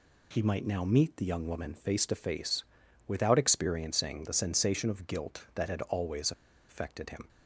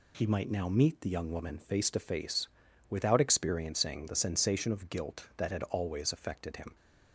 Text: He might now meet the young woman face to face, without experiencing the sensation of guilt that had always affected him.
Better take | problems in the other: second | pauses between "always" and "affected"; at 6.3 s; 0.37 s long

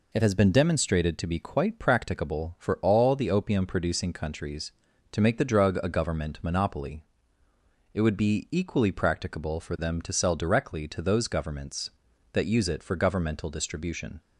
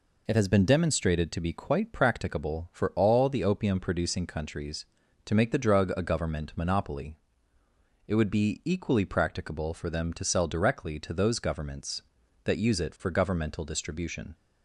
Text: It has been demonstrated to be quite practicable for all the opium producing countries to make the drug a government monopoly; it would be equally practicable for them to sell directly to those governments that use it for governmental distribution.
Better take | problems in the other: neither | none

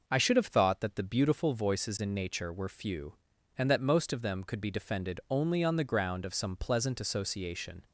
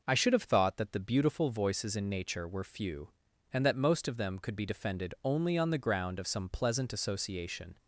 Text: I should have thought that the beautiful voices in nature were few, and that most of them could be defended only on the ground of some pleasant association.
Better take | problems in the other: neither | none

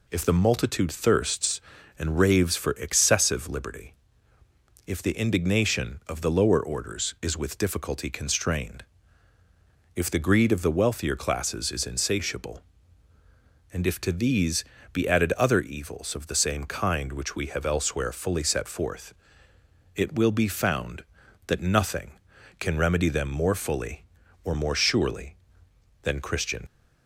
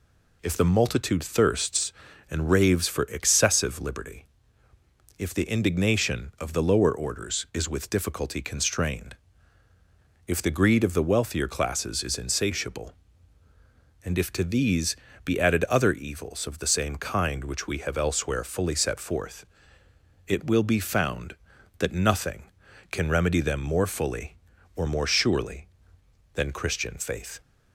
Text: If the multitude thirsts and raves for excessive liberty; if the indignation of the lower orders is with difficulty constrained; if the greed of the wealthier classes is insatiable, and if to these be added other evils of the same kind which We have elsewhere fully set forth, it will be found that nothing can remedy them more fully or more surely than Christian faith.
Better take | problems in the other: second | pauses between "these" and "be"; slight; at 14.6 s; 0.30 s long; slight in the second // stops before "faith"; at 26.6 s

